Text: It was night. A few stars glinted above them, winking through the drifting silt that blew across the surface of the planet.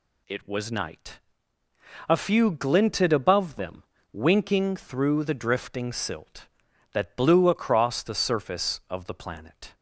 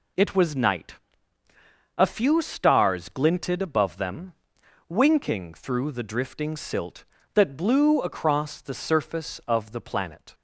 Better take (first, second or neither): second